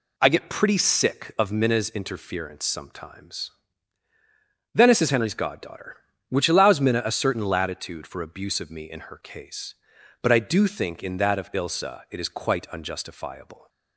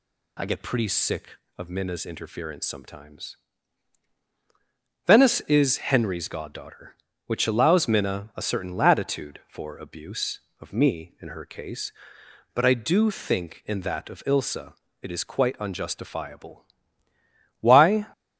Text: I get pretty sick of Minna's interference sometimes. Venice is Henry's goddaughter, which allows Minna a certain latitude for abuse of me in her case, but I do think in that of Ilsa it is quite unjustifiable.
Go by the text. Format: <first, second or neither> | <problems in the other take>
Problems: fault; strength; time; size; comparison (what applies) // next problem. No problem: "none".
first | pauses between "Ilsa" and "it"; slight; at 14.7 s; 0.28 s long // goes on to say "Why"; slight; from 17.5 s on; 0.48 s long